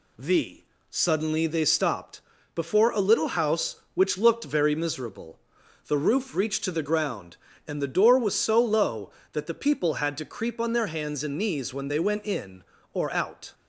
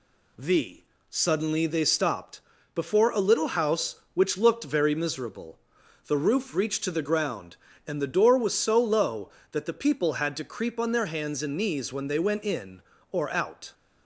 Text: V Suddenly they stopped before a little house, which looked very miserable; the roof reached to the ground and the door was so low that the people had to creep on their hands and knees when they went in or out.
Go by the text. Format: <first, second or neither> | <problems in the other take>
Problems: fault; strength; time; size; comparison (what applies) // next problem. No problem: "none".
neither | pauses between "V" and "Suddenly"; slight; the same in both // pauses between "stopped" and "before"; slight; the same in both